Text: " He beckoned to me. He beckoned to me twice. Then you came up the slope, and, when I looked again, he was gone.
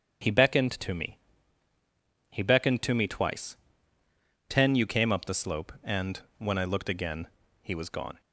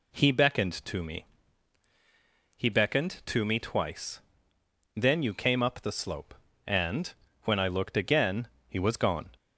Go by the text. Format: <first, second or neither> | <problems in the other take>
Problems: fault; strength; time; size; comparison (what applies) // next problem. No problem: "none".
second | starts louder than the rest; strong; until 2.4 s; 7.5 dB // says "Ten" for "Then"; at 4.4 s